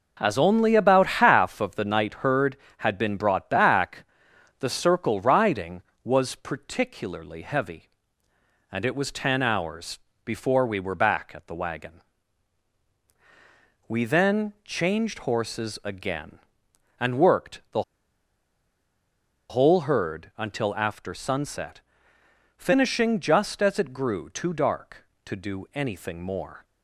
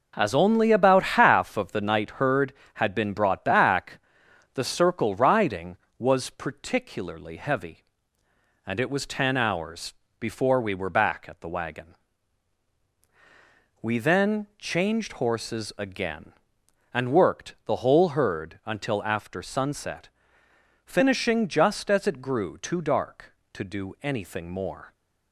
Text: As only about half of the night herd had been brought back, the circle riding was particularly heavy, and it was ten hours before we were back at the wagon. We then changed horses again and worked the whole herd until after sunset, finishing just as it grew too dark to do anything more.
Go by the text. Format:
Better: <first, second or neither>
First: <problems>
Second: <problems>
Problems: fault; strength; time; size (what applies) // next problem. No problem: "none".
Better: second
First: pauses between "hours" and "before"; slight; at 9.9 s; 0.24 s long // pauses between "the" and "whole"; strong; at 17.8 s; 1.6 s long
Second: pauses between "hours" and "before"; slight; at 9.9 s; 0.24 s long